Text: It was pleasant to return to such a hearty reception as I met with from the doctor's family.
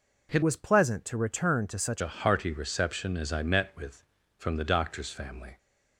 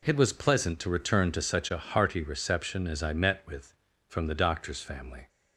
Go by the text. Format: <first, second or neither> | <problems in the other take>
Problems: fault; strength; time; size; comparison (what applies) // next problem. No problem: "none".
second | changes voice from "was" to "such"; from 0.4 to 2.0 s; 1.6 s long